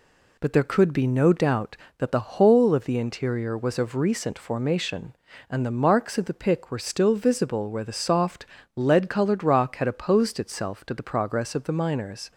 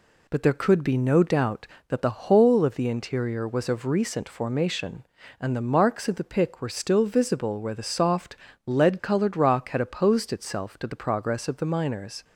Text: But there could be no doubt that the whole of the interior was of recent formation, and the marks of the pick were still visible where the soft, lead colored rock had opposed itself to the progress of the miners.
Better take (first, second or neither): neither